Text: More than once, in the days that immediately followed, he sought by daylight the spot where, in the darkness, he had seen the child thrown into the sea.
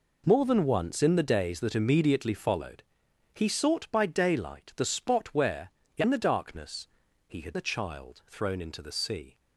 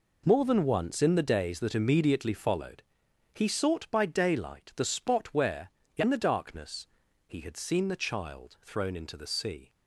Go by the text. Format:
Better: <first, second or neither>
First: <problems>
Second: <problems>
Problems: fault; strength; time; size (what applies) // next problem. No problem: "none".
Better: second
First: skips "seen"; at 7.5 s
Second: none